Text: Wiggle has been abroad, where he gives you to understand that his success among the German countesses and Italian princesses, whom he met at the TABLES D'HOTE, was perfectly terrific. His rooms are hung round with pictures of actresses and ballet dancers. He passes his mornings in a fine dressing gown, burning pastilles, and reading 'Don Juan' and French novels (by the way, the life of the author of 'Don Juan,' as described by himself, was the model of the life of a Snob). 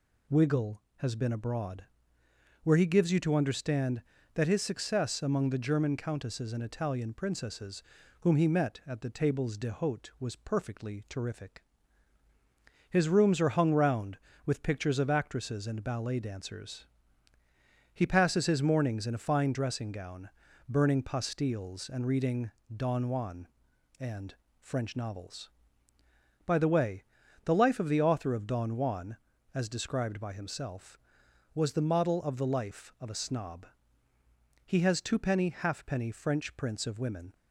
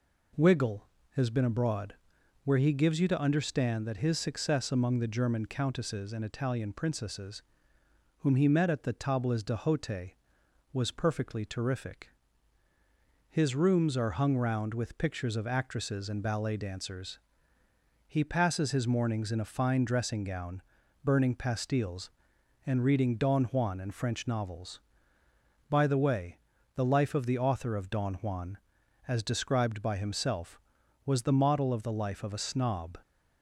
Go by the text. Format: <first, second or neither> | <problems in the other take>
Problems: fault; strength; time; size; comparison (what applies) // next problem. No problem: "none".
second | pauses between "reading" and "Don"; slight; at 22.5 s; 0.24 s long // pauses between "and" and "French"; slight; at 24.3 s; 0.24 s long // goes on to say "He has twopenny halfpenny French prints of women"; strong; from 34.6 s on; 2.7 s long